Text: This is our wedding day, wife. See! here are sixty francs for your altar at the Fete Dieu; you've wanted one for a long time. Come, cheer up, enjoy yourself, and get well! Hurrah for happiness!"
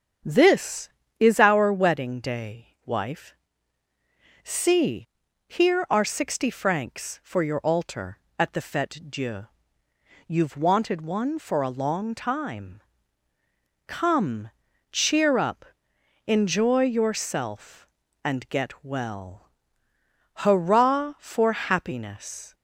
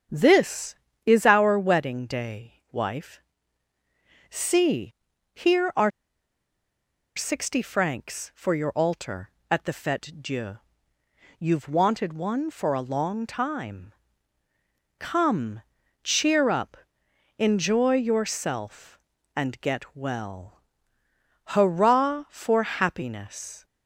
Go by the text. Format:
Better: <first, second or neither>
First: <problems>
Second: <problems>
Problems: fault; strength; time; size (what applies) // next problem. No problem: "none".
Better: first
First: starts louder than the rest; strong; until 1.5 s; 8 dB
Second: starts louder than the rest; strong; until 1.4 s; 8 dB // pauses between "are" and "sixty"; strong; at 5.9 s; 1.2 s long